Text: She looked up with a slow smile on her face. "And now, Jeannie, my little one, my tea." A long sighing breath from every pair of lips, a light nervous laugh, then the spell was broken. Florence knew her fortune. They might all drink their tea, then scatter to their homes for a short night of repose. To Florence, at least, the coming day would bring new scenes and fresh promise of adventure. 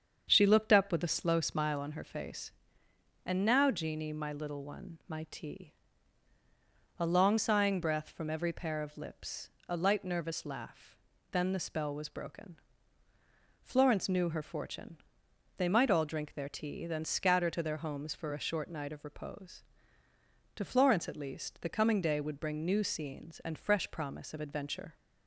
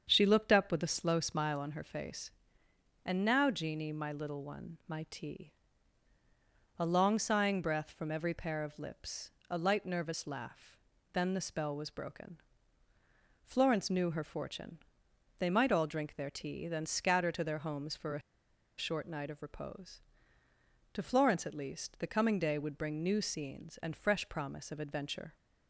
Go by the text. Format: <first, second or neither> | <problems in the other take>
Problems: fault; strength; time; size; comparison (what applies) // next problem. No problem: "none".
first | starts louder than the rest; strong; until 1.1 s; 7 dB; strong in the first // pauses between "a" and "short"; noticeable; at 18.2 s; 0.57 s long